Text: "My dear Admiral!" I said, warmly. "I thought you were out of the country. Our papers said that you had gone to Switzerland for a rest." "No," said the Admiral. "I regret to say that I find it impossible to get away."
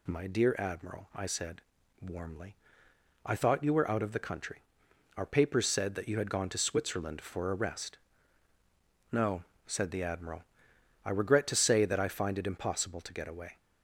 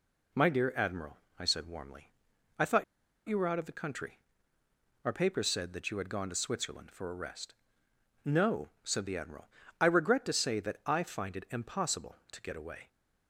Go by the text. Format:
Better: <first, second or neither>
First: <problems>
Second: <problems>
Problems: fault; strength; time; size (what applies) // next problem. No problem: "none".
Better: first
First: none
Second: pauses between "thought" and "you"; at 2.8 s; 0.44 s long